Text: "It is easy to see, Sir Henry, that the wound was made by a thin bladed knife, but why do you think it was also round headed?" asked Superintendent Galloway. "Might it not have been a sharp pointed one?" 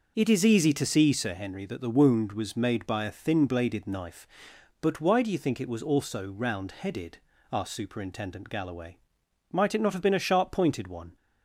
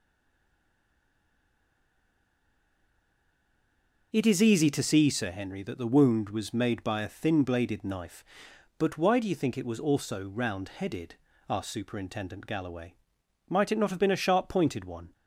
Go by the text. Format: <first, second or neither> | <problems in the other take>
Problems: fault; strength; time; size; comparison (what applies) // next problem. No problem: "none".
first | stays silent before the first word; strong; until 4.1 s; 4.1 s long // starts louder than the rest; noticeable; until 5.1 s; 6 dB